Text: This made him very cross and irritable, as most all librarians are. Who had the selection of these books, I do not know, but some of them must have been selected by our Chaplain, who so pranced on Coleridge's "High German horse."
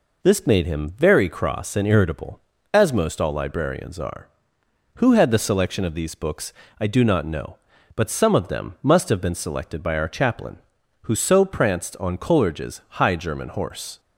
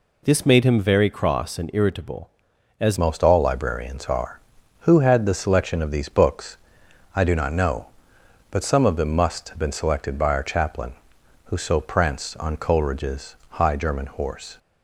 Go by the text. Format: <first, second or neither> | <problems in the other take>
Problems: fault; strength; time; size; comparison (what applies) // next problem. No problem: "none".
first | changes voice at "most"; from 2.9 s on; 11.6 s long // pauses between "Coleridge's" and "High"; slight; at 13.3 s; 0.18 s long